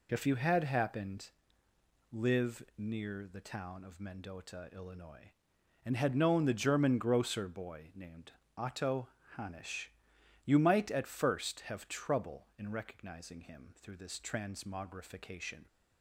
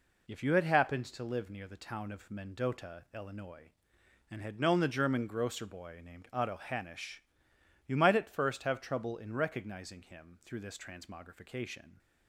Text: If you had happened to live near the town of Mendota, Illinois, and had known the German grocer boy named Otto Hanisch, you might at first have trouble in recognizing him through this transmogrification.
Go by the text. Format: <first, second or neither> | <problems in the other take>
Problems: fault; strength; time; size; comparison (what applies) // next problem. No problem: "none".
second | skips "to"; at 1.6 s // pauses between "named" and "Otto"; slight; at 8.3 s; 0.24 s long // pauses between "Otto" and "Hanisch"; slight; at 9.0 s; 0.30 s long